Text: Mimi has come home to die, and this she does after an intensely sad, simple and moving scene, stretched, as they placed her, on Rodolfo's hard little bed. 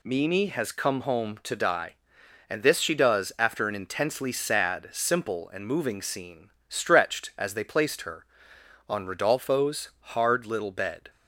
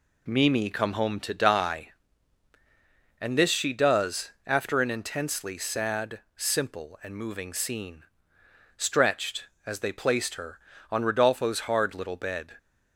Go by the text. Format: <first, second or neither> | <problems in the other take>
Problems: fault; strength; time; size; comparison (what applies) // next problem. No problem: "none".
first | skips "has"; at 0.6 s